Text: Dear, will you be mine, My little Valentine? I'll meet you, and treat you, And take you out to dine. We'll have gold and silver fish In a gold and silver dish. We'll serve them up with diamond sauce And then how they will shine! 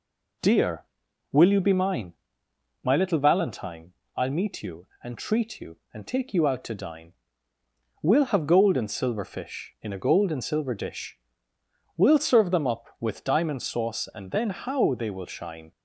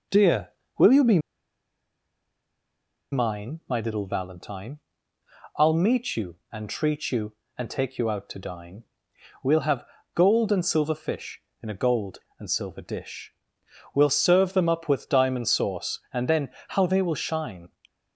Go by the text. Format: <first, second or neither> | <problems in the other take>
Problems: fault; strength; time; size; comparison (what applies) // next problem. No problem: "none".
first | pauses between "be" and "mine"; strong; at 1.1 s; 1.9 s long // pauses between "have" and "gold"; slight; at 9.8 s; 0.30 s long // pauses between "then" and "how"; slight; at 16.4 s; 0.20 s long